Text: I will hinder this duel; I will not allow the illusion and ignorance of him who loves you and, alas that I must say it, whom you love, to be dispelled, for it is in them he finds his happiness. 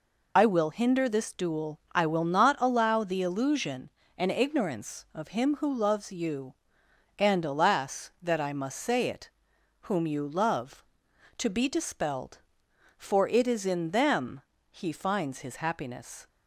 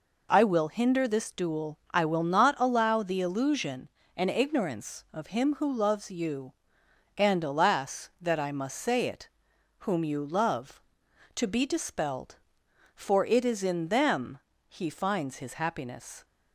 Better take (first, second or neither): second